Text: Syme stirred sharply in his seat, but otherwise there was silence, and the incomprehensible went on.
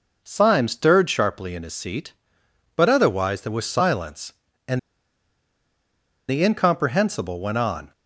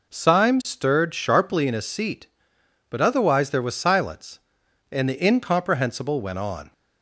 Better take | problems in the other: second | pauses between "and" and "the"; strong; at 4.7 s; 1.4 s long

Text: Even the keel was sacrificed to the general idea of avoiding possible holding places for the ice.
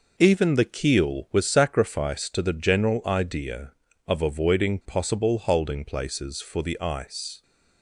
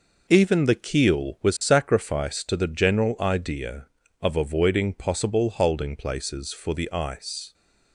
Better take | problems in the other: neither | none

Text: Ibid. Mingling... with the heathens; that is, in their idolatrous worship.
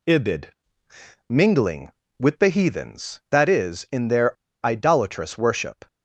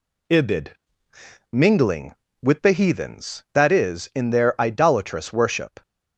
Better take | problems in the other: second | pauses between "their" and "idolatrous"; slight; at 4.3 s; 0.27 s long

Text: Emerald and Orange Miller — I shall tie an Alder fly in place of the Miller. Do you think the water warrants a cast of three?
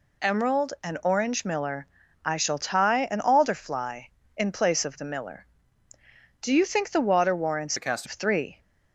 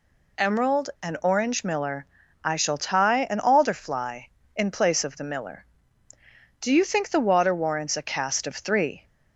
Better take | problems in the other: second | changes voice from "a" to "cast"; from 7.7 to 8.0 s; 0.3 s long

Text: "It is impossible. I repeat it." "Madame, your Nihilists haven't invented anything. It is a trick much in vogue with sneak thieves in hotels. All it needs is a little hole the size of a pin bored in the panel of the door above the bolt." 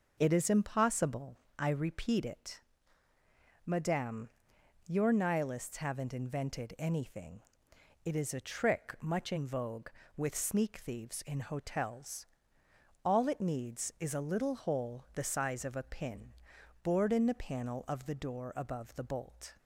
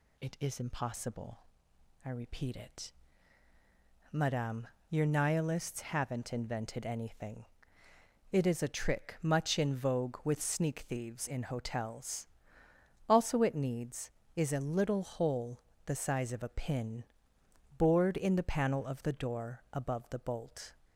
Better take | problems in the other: first | says "Also" for "All"; at 13.0 s // pauses between "hole" and "the"; slight; at 15.6 s; 0.24 s long // pauses between "pin" and "bored"; noticeable; at 17.0 s; 0.72 s long; noticeable in the first

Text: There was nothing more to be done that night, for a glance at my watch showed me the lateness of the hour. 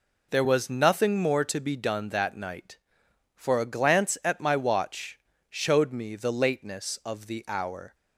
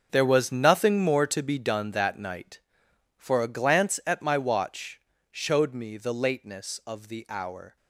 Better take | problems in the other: first | gets quieter; strong; throughout; 13 dB // pauses between "watch" and "showed"; slight; at 4.9 s; 0.30 s long; slight in the first

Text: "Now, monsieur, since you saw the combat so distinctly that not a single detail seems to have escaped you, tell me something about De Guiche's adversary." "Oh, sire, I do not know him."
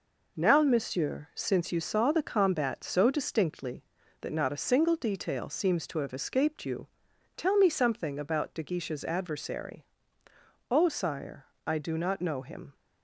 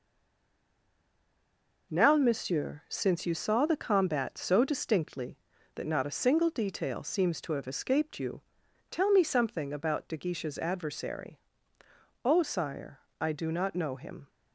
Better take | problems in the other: first | stays silent before the first word; noticeable; until 1.9 s; 1.9 s long

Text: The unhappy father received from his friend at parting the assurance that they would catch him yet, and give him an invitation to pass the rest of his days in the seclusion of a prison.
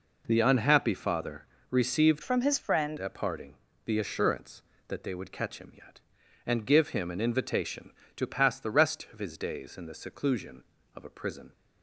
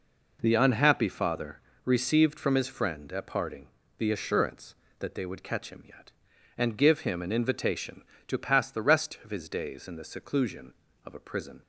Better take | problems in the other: second | pauses between "father" and "received"; slight; at 1.4 s; 0.24 s long; slight in the second // changes voice from "from" to "friend"; from 2.2 to 2.9 s; 0.7 s long // pauses between "parting" and "the"; slight; at 3.5 s; 0.32 s long; slight in the second

